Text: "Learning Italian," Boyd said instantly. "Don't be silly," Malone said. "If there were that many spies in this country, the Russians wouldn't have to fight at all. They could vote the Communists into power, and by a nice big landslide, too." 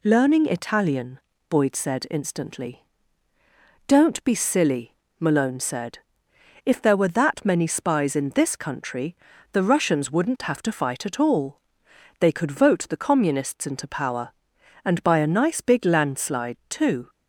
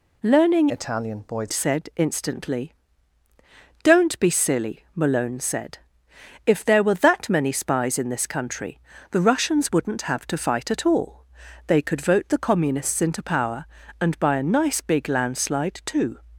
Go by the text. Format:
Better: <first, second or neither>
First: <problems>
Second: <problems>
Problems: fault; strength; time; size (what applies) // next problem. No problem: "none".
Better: first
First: none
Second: changes voice from "Italian" to "Boyd"; from 0.6 to 1.5 s; 0.9 s long